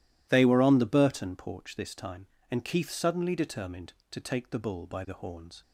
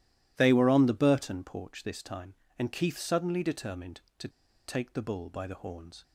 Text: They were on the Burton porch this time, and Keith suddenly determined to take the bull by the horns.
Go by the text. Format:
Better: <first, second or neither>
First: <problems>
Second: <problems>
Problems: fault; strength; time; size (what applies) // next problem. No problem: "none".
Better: first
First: none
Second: pauses between "to" and "take"; at 4.2 s; 0.37 s long